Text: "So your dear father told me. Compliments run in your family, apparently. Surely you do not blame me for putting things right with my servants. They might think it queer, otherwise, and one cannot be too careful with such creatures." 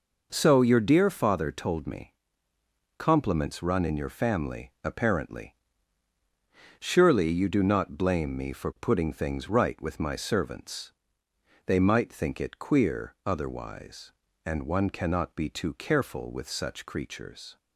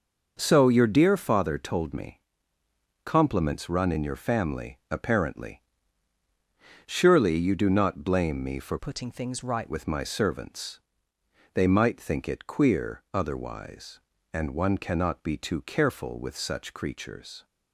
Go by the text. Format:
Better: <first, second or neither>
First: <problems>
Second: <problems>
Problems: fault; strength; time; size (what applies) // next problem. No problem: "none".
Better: first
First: none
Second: changes voice from "putting" to "right"; from 8.7 to 9.6 s; 0.9 s long